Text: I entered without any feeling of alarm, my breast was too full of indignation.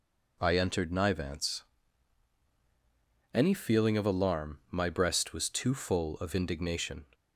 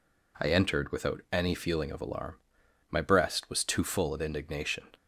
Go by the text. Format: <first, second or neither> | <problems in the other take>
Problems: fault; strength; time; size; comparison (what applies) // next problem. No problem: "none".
second | says "nivance" for "without"; at 0.9 s